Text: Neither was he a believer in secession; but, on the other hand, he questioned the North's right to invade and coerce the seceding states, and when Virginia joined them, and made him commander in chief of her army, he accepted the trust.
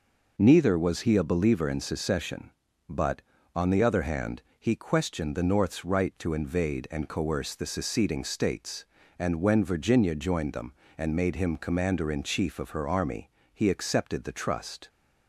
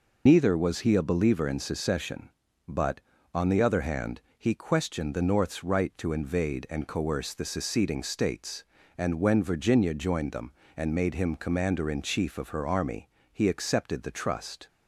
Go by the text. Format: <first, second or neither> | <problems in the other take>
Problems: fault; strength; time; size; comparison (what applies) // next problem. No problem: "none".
first | loses the start of "Neither"; at 0.2 s; 80 ms